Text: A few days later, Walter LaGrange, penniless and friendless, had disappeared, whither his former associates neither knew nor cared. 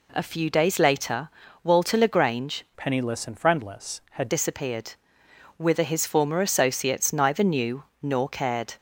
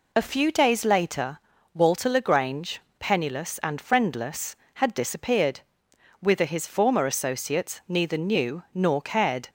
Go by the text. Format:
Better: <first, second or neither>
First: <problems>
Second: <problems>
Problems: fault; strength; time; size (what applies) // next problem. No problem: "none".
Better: second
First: changes voice from "penniless" to "had"; from 2.7 to 4.2 s; 1.5 s long // pauses between "knew" and "nor"; slight; at 7.8 s; 0.18 s long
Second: none